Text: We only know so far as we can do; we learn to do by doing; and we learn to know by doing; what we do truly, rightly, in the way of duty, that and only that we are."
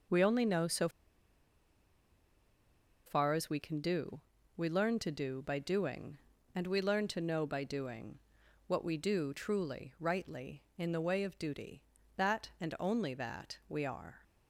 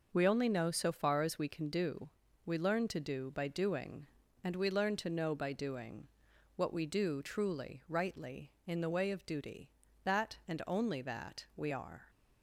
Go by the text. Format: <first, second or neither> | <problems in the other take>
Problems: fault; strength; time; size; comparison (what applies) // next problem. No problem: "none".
second | starts louder than the rest; noticeable; until 3.2 s; 6 dB // pauses between "so" and "far"; strong; at 0.8 s; 2.1 s long